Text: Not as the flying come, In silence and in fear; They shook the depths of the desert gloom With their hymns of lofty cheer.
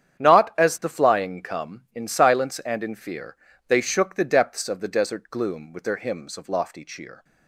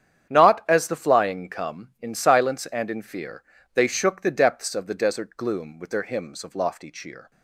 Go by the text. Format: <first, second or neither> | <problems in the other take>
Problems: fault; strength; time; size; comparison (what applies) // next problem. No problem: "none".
neither | starts louder than the rest; strong; the same in both